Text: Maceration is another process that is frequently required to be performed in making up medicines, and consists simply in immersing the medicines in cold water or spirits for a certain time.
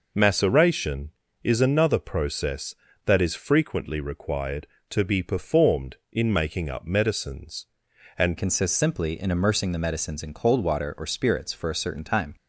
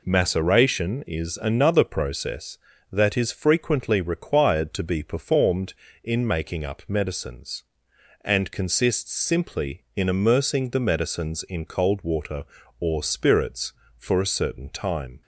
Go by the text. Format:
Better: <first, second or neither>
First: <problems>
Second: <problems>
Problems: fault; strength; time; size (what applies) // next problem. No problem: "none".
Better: second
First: changes voice at "consists"; from 8.3 s on; 4.0 s long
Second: none